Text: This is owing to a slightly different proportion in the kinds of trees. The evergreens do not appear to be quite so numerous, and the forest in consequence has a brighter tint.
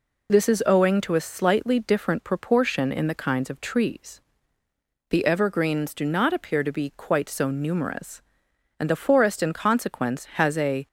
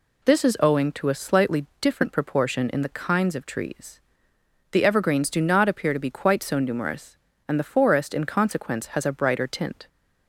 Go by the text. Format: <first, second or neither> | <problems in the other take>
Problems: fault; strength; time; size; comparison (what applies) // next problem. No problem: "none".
second | stops before "brighter tint"; at 10.8 s